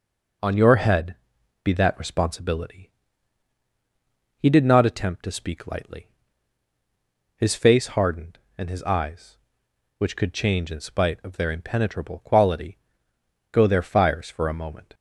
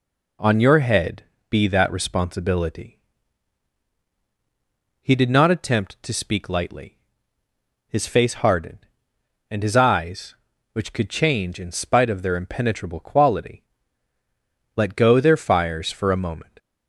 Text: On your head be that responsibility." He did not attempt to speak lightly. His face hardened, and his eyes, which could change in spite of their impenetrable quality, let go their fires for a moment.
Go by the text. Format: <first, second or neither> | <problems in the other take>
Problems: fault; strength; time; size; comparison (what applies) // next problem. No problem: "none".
second | pauses between "head" and "be"; noticeable; at 1.1 s; 0.48 s long; slight in the second // skips "let"; at 13.1 s